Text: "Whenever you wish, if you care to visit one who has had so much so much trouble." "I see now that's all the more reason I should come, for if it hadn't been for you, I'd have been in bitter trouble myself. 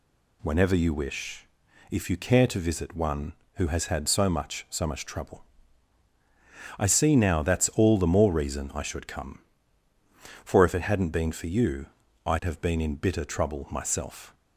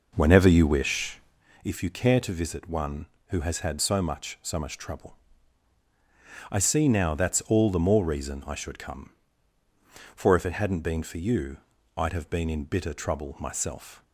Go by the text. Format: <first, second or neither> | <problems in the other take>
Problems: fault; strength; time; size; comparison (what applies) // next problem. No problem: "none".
first | starts louder than the rest; noticeable; until 1.4 s; 5.5 dB